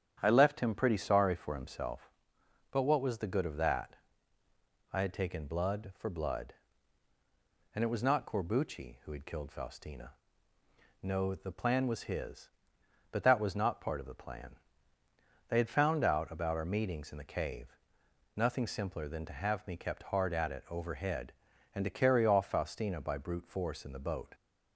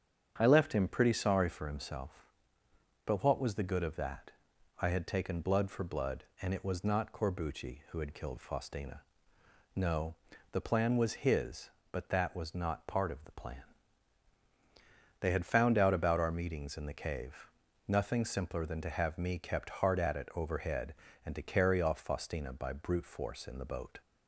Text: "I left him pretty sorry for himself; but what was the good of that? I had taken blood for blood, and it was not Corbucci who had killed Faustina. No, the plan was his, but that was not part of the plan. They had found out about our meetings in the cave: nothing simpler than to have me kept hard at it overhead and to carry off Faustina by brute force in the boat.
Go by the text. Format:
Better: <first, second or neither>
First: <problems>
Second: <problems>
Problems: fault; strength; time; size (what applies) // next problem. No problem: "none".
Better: neither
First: starts louder than the rest; strong; until 1.2 s; 9 dB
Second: starts louder than the rest; strong; until 1.3 s; 8 dB